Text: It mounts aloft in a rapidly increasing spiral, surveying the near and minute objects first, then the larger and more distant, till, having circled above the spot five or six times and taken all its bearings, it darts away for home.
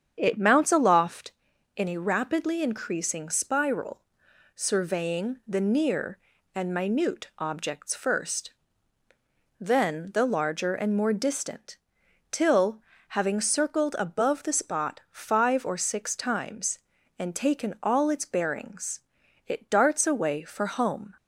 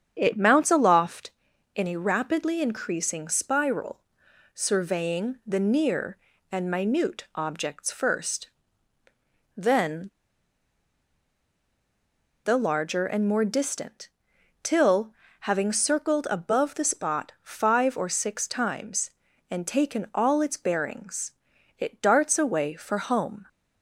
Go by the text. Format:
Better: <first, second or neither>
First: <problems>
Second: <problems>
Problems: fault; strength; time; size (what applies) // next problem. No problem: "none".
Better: first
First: starts louder than the rest; strong; until 1.1 s; 8 dB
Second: starts louder than the rest; strong; until 1.1 s; 8 dB // pauses between "then" and "the"; strong; at 10.0 s; 2.3 s long